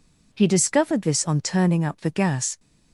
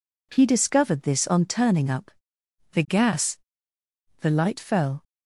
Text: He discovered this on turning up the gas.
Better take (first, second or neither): first